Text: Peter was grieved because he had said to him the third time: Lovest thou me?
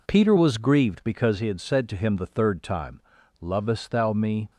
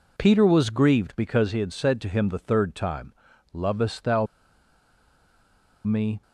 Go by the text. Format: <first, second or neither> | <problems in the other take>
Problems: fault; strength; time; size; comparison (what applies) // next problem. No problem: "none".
first | pauses between "thou" and "me"; strong; at 4.2 s; 1.5 s long